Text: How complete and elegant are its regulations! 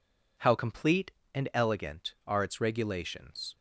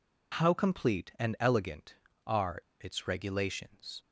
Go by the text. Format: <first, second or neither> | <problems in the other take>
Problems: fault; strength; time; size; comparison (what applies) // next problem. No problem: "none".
first | pauses between "are" and "its"; slight; at 2.5 s; 0.21 s long